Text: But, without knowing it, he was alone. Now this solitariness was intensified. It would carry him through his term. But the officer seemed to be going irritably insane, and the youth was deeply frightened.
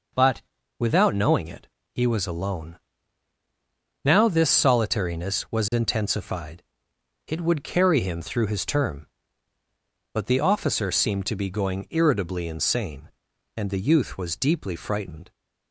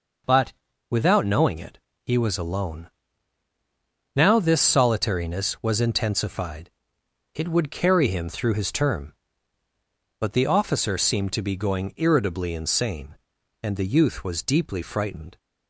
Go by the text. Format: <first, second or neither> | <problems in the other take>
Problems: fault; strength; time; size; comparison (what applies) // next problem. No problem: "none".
neither | none